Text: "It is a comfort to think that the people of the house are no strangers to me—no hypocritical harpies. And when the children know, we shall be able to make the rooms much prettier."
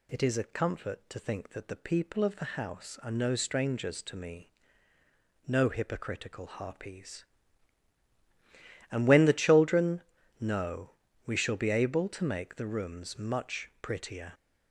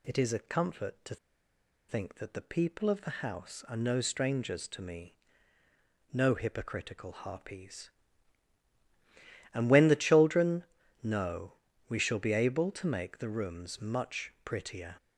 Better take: first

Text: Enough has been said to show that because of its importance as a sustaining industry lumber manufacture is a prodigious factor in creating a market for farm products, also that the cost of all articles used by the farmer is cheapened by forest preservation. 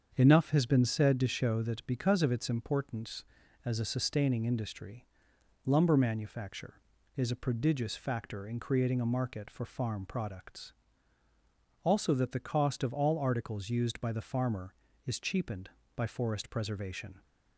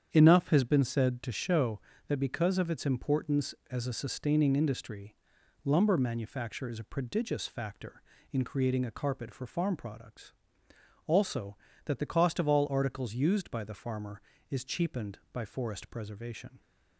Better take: first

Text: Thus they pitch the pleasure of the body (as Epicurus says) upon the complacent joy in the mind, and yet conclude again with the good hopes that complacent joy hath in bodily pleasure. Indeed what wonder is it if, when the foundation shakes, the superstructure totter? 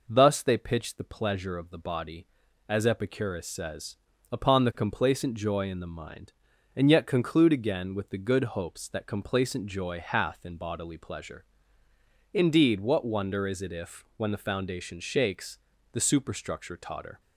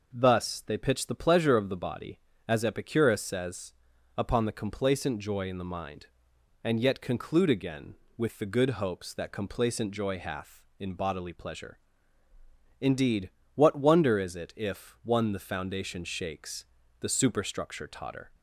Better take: first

